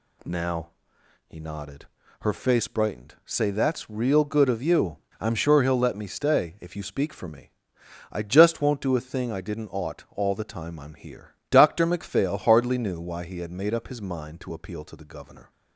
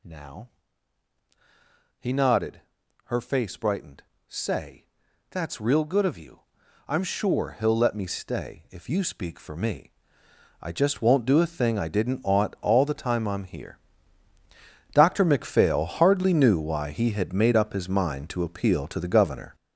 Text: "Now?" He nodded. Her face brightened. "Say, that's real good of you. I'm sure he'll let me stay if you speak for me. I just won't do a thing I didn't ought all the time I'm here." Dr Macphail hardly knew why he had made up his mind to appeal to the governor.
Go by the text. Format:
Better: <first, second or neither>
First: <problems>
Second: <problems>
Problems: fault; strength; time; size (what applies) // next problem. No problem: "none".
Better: first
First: none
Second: gets louder; strong; throughout; 8.5 dB